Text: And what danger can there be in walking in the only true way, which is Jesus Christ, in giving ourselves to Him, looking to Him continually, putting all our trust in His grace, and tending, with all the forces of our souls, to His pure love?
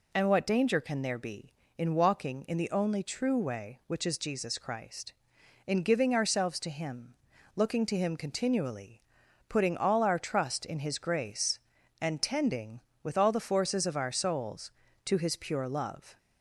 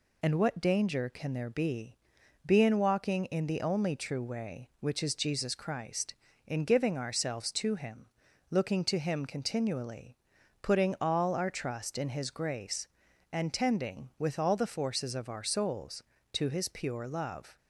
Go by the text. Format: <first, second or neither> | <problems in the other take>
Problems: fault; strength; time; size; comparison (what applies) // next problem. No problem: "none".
first | says "be" twice; at 2.4 s